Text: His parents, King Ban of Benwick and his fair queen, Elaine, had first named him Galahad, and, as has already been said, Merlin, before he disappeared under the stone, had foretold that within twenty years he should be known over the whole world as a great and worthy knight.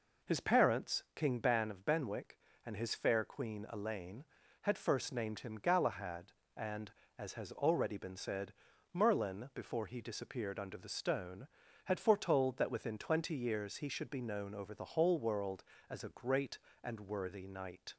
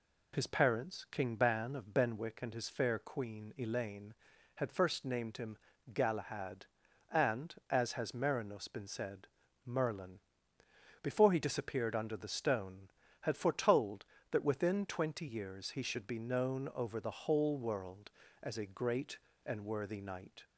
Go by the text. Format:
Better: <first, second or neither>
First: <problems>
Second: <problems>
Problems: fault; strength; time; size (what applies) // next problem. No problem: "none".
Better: first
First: none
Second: pauses between "him" and "Galahad"; slight; at 5.5 s; 0.36 s long // says "merinos" for "already"; at 8.1 s